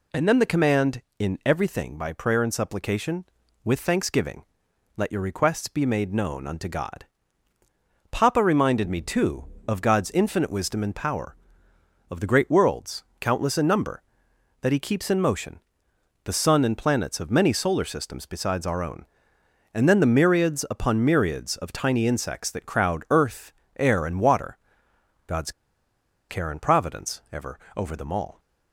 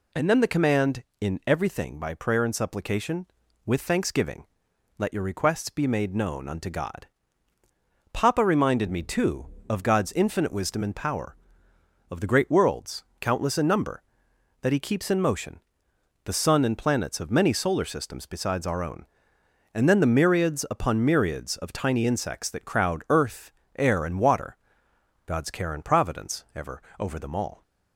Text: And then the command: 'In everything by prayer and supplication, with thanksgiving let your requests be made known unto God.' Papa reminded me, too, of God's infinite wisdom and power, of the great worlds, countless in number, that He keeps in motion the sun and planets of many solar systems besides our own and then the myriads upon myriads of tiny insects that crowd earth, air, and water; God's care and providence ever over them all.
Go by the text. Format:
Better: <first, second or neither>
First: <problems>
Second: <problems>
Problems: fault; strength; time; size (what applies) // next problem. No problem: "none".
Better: second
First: pauses between "thanksgiving" and "let"; noticeable; at 4.4 s; 0.52 s long // pauses between "motion" and "the"; noticeable; at 15.5 s; 0.66 s long // pauses between "God's" and "care"; noticeable; at 25.5 s; 0.78 s long // pauses between "ever" and "over"; slight; at 27.5 s; 0.16 s long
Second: pauses between "thanksgiving" and "let"; noticeable; at 4.4 s; 0.52 s long // pauses between "motion" and "the"; noticeable; at 15.5 s; 0.66 s long // pauses between "ever" and "over"; slight; at 26.8 s; 0.16 s long